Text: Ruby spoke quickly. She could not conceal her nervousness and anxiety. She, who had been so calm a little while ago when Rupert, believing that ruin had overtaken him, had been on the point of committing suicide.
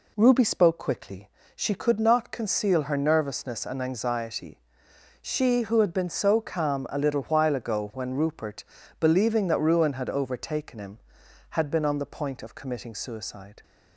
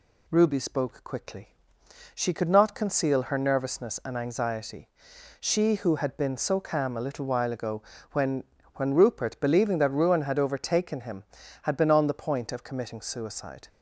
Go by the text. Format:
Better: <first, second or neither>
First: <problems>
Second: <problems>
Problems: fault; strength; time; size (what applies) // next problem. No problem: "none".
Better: first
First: none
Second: pauses between "ago" and "when"; slight; at 7.8 s; 0.30 s long // says "when" twice; at 8.7 s